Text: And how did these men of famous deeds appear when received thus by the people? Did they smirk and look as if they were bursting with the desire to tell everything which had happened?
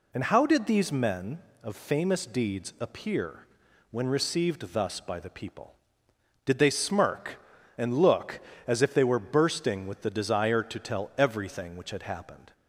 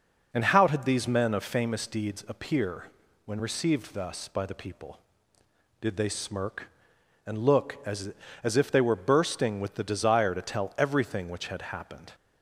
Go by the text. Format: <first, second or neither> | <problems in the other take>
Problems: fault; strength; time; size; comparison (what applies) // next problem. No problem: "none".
first | pauses between "appear" and "when"; at 2.8 s; 0.40 s long; also in the first // says "as" twice; at 8.4 s